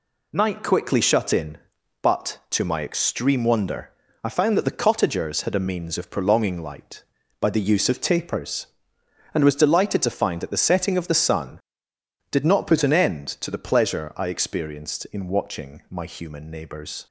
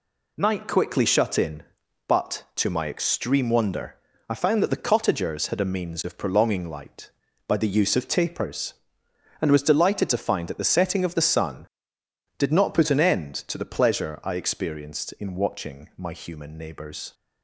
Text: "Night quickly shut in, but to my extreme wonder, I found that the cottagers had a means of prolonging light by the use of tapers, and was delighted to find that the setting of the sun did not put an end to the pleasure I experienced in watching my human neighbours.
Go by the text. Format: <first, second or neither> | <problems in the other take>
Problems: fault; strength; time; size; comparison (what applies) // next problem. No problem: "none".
neither | none